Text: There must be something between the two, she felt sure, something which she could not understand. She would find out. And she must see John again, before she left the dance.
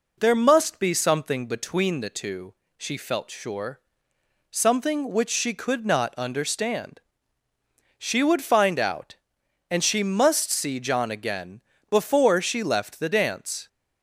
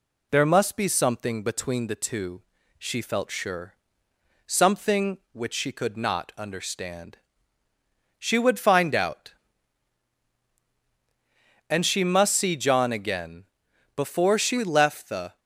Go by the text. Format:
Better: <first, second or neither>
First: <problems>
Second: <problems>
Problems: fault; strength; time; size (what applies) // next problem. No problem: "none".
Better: first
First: none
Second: stops before "dance"; at 15.3 s